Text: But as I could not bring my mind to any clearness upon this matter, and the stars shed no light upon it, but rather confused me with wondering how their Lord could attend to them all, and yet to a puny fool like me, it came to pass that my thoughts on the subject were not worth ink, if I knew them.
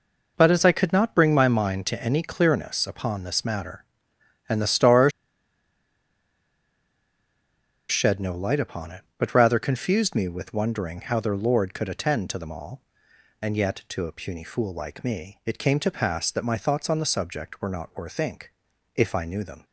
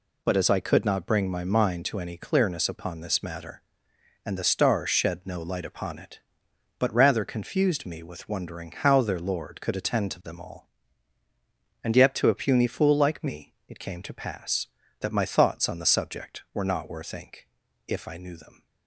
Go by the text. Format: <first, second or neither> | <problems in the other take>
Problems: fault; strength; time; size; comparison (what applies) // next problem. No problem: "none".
second | pauses between "stars" and "shed"; strong; at 5.1 s; 2.7 s long